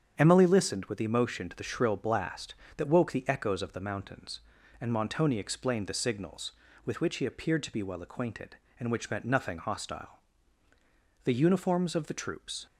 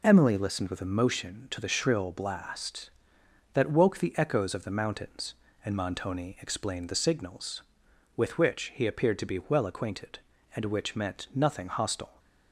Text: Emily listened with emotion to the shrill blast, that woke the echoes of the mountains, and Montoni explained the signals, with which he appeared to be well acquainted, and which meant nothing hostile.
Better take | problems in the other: second | starts louder than the rest; strong; until 1.1 s; 7.5 dB // goes on to say "The uniforms of the troops"; from 11.2 s on; 1.4 s long

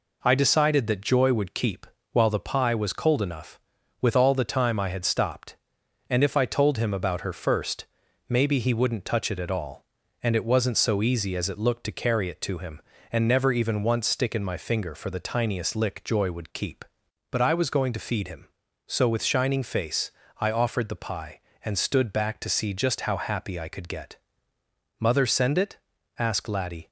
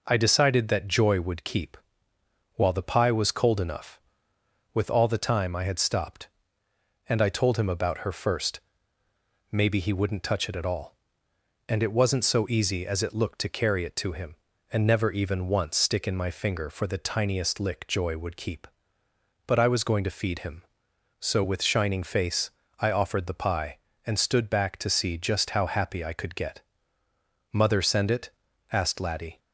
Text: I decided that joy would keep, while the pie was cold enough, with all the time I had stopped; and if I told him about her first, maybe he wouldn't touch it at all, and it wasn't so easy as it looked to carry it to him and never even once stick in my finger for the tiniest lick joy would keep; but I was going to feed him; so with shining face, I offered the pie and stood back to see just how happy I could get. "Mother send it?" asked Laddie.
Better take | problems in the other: first | skips "if"; at 7.2 s

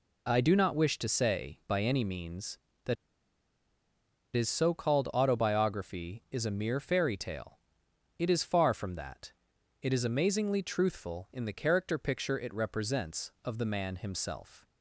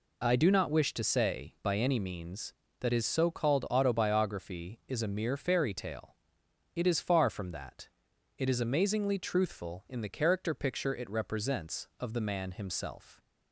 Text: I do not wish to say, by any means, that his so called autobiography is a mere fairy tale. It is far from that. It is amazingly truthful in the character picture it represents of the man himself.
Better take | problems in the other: second | pauses between "that" and "his"; strong; at 2.9 s; 1.4 s long

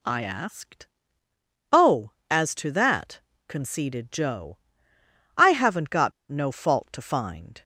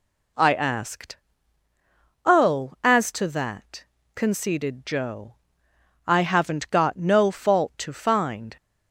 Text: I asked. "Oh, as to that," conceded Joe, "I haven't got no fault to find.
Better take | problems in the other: second | pauses between "got" and "no"; slight; at 6.1 s; 0.17 s long

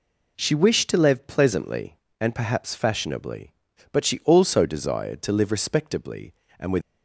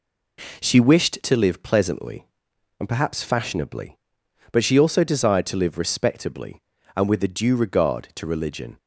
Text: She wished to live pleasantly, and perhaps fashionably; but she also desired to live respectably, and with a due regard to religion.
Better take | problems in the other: second | stops before "a due regard to religion"; at 6.8 s

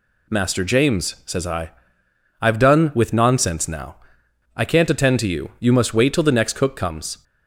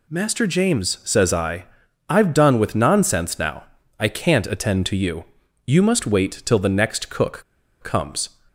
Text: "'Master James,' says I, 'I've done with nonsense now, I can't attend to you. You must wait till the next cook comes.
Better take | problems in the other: first | pauses between "cook" and "comes"; at 7.4 s; 0.40 s long

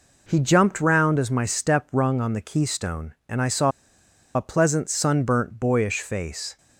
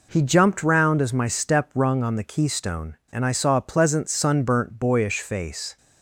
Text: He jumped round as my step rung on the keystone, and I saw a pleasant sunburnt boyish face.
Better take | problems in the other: second | pauses between "saw" and "a"; noticeable; at 3.7 s; 0.64 s long

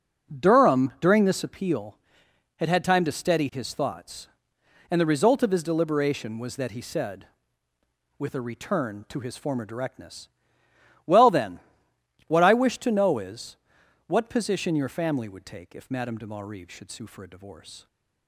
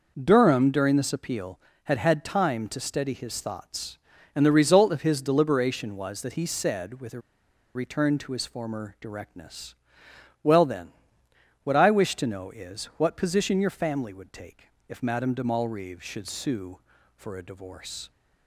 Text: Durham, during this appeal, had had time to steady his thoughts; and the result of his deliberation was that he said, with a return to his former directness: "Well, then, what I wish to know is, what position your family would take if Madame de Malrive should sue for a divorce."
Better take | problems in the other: first | pauses between "a" and "return"; noticeable; at 7.2 s; 0.54 s long // pauses between "take" and "if"; slight; at 14.6 s; 0.24 s long

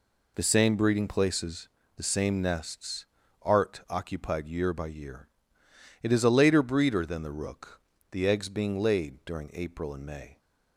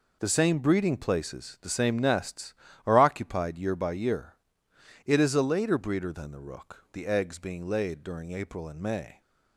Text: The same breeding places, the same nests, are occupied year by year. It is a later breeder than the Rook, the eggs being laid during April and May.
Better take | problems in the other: second | says "art" for "are"; at 3.4 s

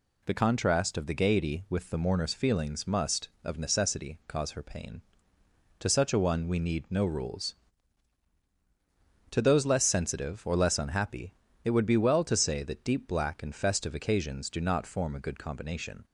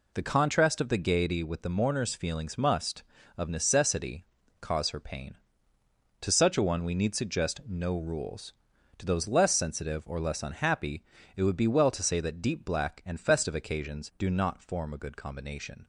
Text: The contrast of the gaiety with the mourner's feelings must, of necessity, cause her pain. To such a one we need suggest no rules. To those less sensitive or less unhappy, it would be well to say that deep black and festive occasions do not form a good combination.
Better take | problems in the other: second | skips "suggest"; at 6.8 s

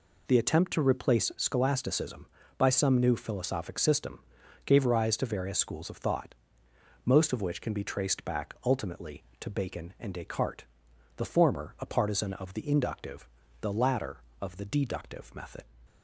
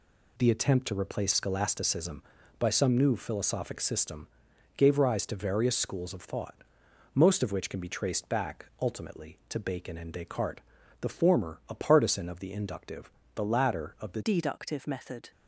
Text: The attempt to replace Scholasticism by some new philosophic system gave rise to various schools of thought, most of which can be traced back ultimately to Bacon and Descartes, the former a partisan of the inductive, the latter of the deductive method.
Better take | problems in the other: first | pauses between "system" and "gave"; noticeable; at 4.2 s; 0.48 s long; noticeable in the first // pauses between "back" and "ultimately"; slight; at 8.6 s; 0.16 s long // changes voice at "deductive"; from 14.2 s on; 1.1 s long

